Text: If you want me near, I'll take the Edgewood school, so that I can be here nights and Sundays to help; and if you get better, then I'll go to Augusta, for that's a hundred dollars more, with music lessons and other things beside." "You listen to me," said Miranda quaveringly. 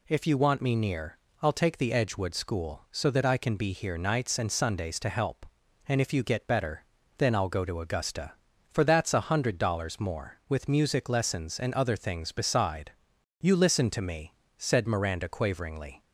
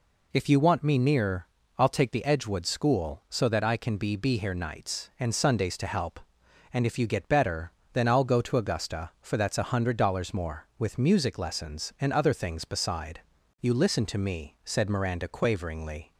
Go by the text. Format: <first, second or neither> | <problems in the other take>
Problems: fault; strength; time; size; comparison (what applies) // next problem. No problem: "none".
first | says "be" twice; at 4.1 s